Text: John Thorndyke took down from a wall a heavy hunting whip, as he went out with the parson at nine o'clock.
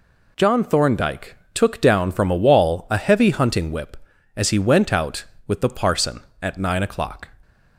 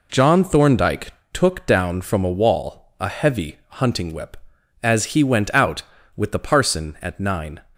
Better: first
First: pauses between "Thorndyke" and "took"; slight; at 1.3 s; 0.16 s long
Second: pauses between "Thorndyke" and "took"; slight; at 1.1 s; 0.20 s long // stops before "o'clock"; at 7.7 s

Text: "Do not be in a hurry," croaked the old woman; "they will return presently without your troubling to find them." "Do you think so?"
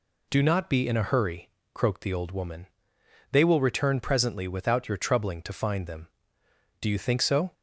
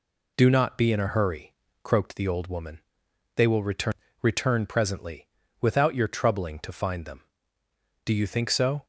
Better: first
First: none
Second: says "return" twice; at 4.2 s // pauses between "presently" and "without"; slight; at 5.2 s; 0.34 s long

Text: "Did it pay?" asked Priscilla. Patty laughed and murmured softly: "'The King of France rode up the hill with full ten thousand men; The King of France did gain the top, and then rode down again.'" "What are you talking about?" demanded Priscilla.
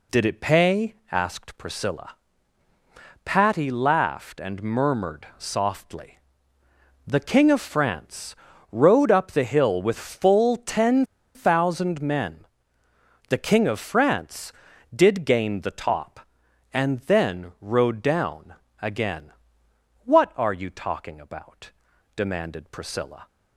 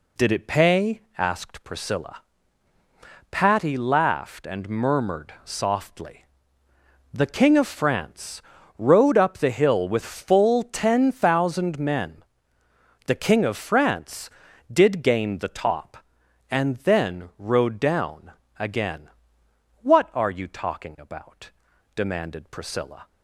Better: second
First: pauses between "France" and "rode"; at 8.3 s; 0.38 s long // pauses between "ten" and "thousand"; slight; at 11.0 s; 0.30 s long // pauses between "down" and "again"; slight; at 18.5 s; 0.28 s long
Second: pauses between "France" and "rode"; at 8.4 s; 0.38 s long // pauses between "down" and "again"; slight; at 18.3 s; 0.28 s long

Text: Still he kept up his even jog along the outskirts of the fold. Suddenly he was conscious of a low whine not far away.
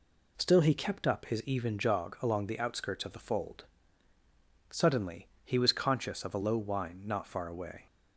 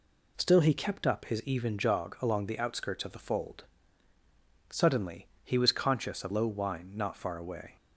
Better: first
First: pauses between "Suddenly" and "he"; slight; at 5.2 s; 0.16 s long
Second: pauses between "Suddenly" and "he"; slight; at 5.2 s; 0.16 s long // skips "a"; at 6.3 s

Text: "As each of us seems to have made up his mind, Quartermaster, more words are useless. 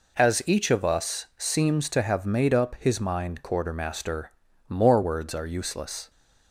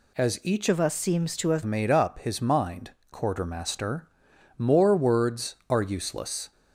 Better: first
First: none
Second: changes voice from "of" to "have"; from 0.6 to 1.6 s; 1.0 s long

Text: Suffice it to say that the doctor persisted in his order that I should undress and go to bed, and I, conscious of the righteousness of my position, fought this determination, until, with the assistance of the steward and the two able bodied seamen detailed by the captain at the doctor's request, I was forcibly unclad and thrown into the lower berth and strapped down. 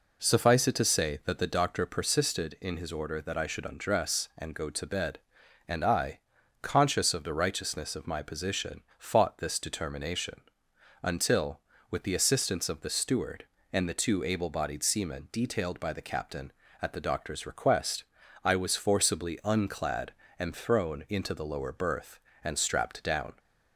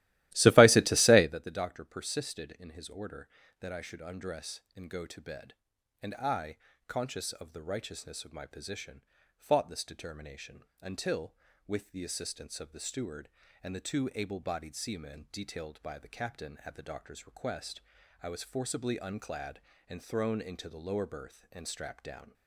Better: first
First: none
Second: starts louder than the rest; strong; until 1.4 s; 16 dB

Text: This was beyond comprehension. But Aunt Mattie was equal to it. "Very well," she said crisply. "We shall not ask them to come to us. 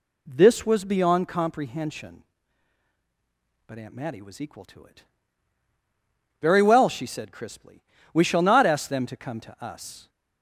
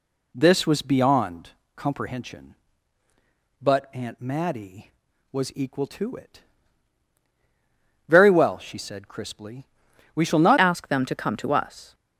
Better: first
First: none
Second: pauses between "beyond" and "comprehension"; slight; at 1.5 s; 0.26 s long // changes voice at "ask"; from 10.5 s on; 1.4 s long

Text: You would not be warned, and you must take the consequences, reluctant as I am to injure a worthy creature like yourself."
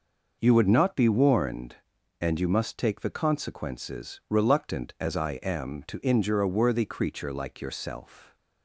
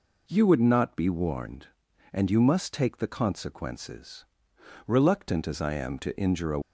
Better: first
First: none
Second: stops before "worthy creature like yourself"; at 6.6 s

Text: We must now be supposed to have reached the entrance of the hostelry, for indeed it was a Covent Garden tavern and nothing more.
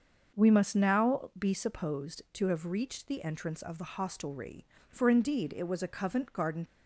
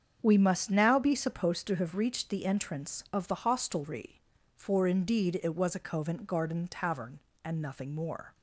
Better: second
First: starts louder than the rest; until 1.4 s; 6.5 dB // stops before "tavern and nothing more"; at 6.6 s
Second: starts louder than the rest; strong; until 1.2 s; 7.5 dB

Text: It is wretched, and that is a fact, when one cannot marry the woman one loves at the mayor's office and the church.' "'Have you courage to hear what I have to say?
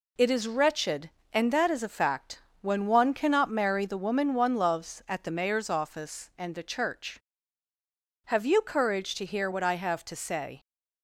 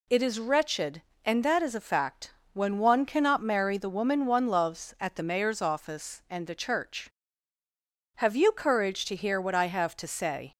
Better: second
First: gets quieter; noticeable; throughout; 4.5 dB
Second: none

